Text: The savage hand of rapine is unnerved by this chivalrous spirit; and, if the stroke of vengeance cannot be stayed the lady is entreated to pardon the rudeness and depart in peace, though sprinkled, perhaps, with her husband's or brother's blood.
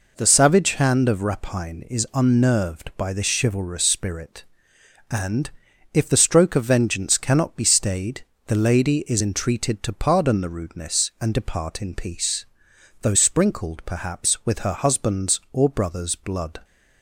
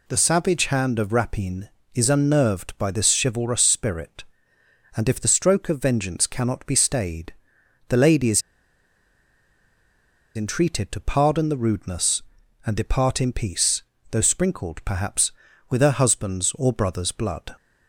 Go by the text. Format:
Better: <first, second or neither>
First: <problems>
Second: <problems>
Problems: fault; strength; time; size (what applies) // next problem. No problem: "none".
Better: first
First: pauses between "stayed" and "the"; slight; at 8.2 s; 0.24 s long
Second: pauses between "stayed" and "the"; noticeable; at 7.3 s; 0.54 s long // pauses between "is" and "entreated"; strong; at 8.3 s; 1.9 s long